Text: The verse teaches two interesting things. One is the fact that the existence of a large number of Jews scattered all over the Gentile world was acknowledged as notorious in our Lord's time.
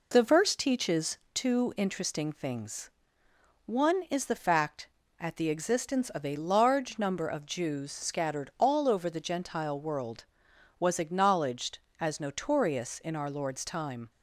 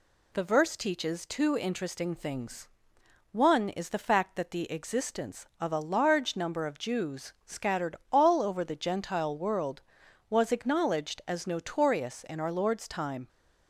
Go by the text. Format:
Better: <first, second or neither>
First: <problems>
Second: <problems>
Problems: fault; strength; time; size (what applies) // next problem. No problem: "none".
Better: second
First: pauses between "teaches" and "two"; slight; at 1.1 s; 0.16 s long // says "at" for "that"; at 5.1 s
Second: none